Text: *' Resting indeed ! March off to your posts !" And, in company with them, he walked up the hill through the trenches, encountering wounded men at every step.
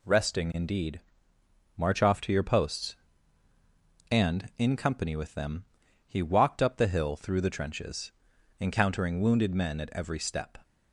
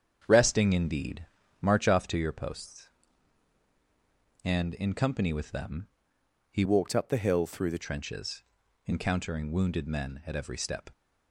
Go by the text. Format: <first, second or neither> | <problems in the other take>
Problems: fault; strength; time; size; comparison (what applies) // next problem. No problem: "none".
first | starts louder than the rest; strong; until 1.2 s; 7.5 dB // changes voice from "walked" to "the"; from 6.6 to 7.8 s; 1.2 s long